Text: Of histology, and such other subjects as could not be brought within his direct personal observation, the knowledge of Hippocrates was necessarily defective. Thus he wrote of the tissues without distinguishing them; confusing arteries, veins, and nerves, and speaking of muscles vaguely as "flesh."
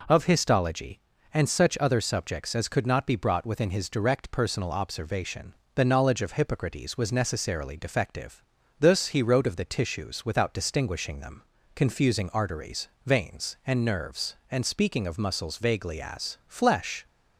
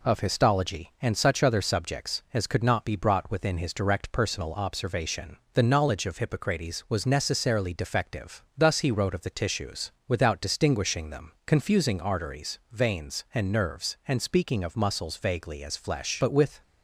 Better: first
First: none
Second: pauses between "tissues" and "without"; slight; at 9.9 s; 0.16 s long // goes on to say "But with"; slight; from 16.1 s on; 0.42 s long

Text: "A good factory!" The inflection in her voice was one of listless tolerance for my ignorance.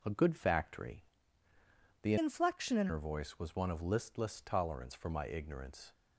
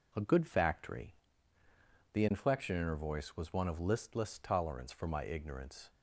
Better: second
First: changes voice from "inflection" to "in"; from 2.1 to 2.8 s; 0.7 s long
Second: none

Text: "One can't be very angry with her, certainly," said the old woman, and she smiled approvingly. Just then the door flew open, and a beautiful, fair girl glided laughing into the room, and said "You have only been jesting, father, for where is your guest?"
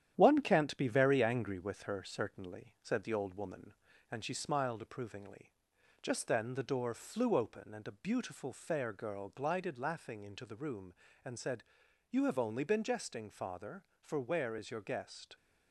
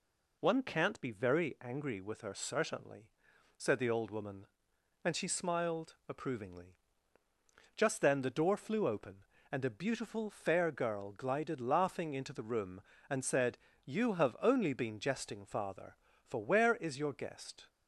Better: second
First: gets quieter; noticeable; throughout; 5.5 dB // pauses between "said" and "You"; at 11.6 s; 0.44 s long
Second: pauses between "said" and "You"; slight; at 13.5 s; 0.26 s long

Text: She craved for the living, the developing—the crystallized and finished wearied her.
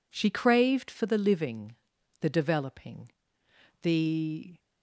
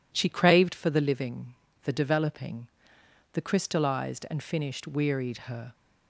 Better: second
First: stops before "crystallized and finished wearied her"; at 4.5 s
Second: none

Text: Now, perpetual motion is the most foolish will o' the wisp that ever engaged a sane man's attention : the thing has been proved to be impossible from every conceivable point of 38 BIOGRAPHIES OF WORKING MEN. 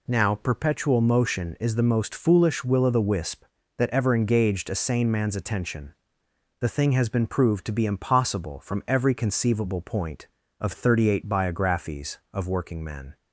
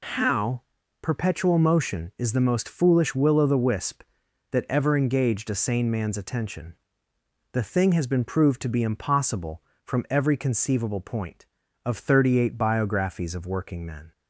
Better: first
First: none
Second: says "How" for "Now"; at 0.0 s

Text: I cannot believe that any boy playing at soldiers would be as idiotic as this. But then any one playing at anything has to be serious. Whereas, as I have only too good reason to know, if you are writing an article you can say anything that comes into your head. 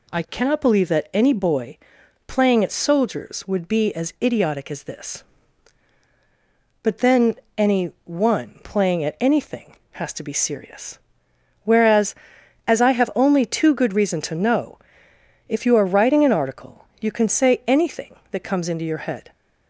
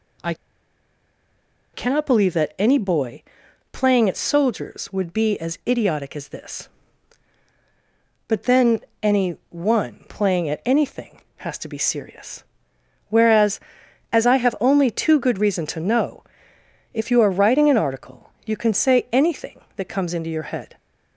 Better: first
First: pauses between "boy" and "playing"; noticeable; at 1.7 s; 0.50 s long // pauses between "then" and "any"; slight; at 7.3 s; 0.20 s long // pauses between "article" and "you"; slight; at 16.8 s; 0.16 s long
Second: pauses between "I" and "cannot"; strong; at 0.3 s; 1.3 s long // pauses between "boy" and "playing"; noticeable; at 3.2 s; 0.50 s long // pauses between "then" and "any"; slight; at 8.8 s; 0.20 s long // pauses between "article" and "you"; slight; at 18.2 s; 0.16 s long

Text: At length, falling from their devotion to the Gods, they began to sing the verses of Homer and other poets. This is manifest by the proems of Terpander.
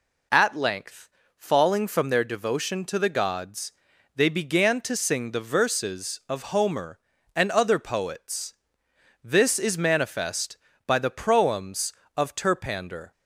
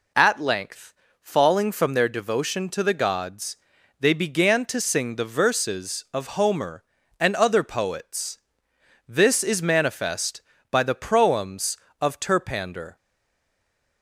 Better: first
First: none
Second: stays silent after the last word; from 12.9 s on; 1.1 s long

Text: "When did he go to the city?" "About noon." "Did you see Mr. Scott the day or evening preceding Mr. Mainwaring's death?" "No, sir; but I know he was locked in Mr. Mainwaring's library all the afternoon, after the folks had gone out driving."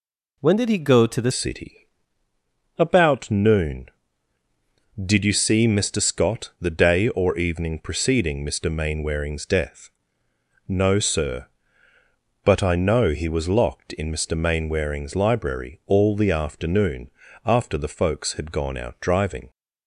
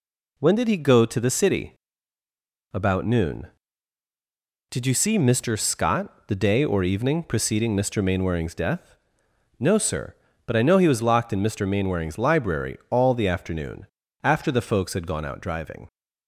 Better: second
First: changes voice at "city"; from 1.3 s on; 18.1 s long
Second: none

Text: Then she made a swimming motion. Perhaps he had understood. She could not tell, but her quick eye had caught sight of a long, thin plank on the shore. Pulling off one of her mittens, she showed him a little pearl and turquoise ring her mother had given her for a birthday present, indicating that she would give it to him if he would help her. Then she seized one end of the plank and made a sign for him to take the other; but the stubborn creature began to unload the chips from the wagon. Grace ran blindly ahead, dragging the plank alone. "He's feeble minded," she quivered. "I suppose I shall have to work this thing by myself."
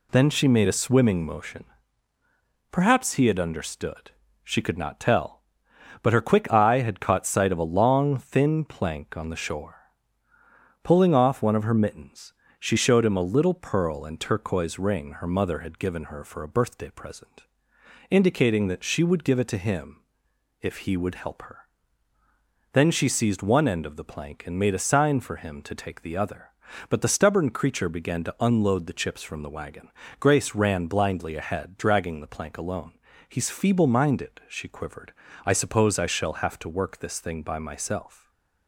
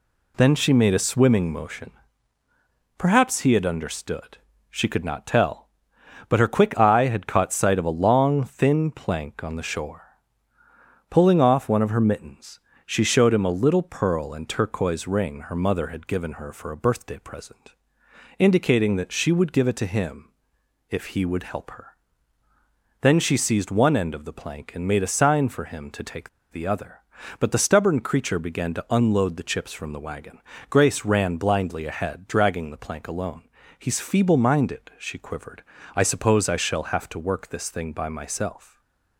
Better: first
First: pauses between "him" and "if"; noticeable; at 20.0 s; 0.60 s long // stays silent after the last word; slight; from 38.1 s on; 0.5 s long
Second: pauses between "him" and "if"; noticeable; at 20.3 s; 0.60 s long // pauses between "take" and "the"; slight; at 26.2 s; 0.22 s long // stays silent after the last word; slight; from 38.6 s on; 0.5 s long

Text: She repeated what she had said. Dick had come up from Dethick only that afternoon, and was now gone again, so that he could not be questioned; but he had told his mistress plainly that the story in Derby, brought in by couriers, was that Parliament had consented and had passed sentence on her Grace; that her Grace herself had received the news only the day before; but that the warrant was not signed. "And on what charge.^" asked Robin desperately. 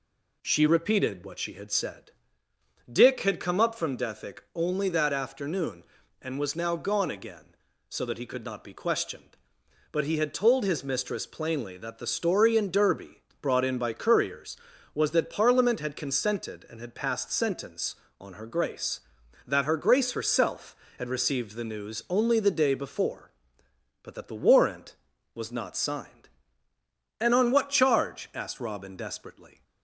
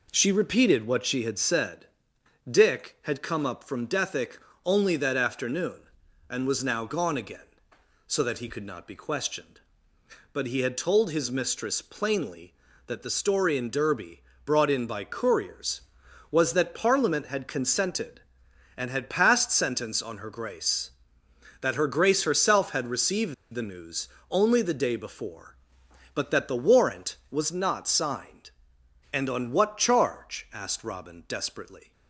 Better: first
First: none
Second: pauses between "Dethick" and "only"; slight; at 4.3 s; 0.26 s long // pauses between "received" and "the"; slight; at 23.3 s; 0.19 s long // pauses between "news" and "only"; slight; at 24.0 s; 0.24 s long

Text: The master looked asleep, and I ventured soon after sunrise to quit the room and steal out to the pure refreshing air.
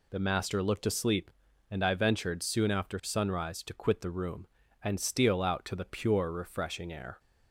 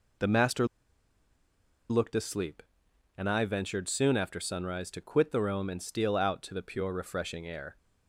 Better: first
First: none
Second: pauses between "master" and "looked"; strong; at 0.6 s; 1.2 s long

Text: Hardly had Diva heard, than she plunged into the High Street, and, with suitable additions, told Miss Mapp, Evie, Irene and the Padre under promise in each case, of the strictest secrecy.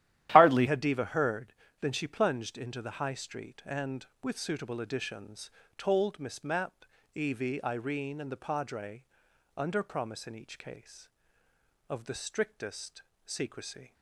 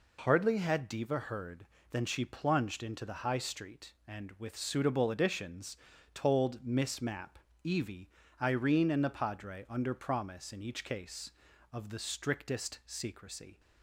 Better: second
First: starts louder than the rest; strong; until 1.3 s; 12.5 dB // changes voice at "had"; from 0.6 s on; 13.3 s long // pauses between "Padre" and "under"; noticeable; at 9.0 s; 0.52 s long // pauses between "strictest" and "secrecy"; slight; at 13.0 s; 0.22 s long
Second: none

